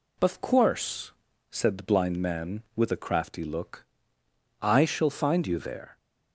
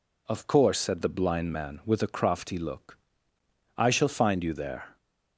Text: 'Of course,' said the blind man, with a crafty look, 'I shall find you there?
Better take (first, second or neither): neither